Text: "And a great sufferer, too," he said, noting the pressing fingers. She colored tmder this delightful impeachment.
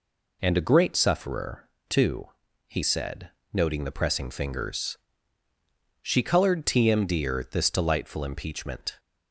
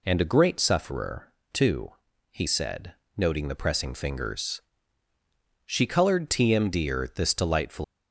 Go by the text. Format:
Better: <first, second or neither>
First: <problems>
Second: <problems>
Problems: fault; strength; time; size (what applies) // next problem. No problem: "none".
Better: first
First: none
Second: stops before "impeachment"; at 7.8 s